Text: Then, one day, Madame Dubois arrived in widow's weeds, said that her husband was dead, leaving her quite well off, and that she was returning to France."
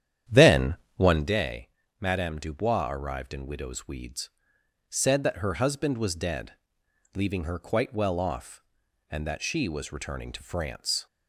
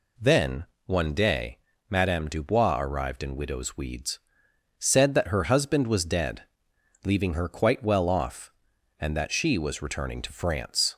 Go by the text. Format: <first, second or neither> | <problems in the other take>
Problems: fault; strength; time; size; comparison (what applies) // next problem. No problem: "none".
second | starts louder than the rest; strong; until 1.4 s; 10 dB